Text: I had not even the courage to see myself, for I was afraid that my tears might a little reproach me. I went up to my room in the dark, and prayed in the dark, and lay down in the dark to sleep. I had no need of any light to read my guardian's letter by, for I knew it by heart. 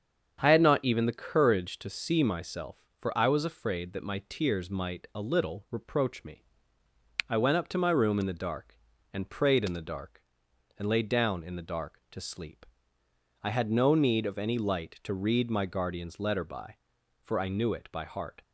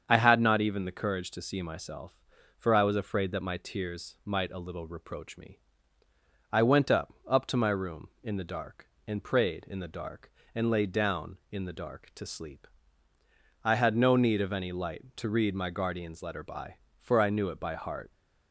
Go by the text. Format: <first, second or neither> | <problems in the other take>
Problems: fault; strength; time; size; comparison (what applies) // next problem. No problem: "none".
first | starts louder than the rest; strong; until 1.0 s; 7.5 dB; strong in the first // says "up" twice; at 7.2 s